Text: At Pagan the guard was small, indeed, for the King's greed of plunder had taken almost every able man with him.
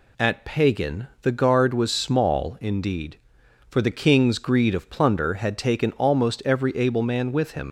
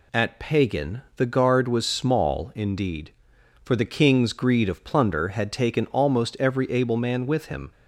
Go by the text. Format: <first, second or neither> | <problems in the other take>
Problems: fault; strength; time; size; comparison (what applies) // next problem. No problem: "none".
second | leaves "him" unfinished; at 7.6 s; 65 ms